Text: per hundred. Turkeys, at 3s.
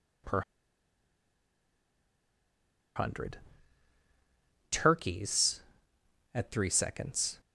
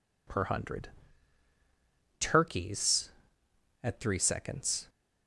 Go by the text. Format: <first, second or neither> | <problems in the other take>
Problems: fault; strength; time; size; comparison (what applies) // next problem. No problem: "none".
second | pauses between "per" and "hundred"; strong; at 0.4 s; 2.5 s long